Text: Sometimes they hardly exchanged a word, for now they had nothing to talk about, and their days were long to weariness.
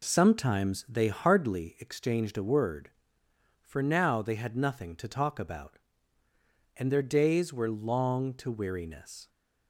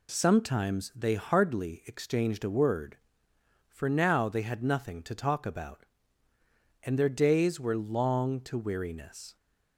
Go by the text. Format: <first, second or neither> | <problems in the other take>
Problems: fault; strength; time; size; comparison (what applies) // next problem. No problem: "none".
second | starts louder than the rest; slight; until 1.8 s; 3.5 dB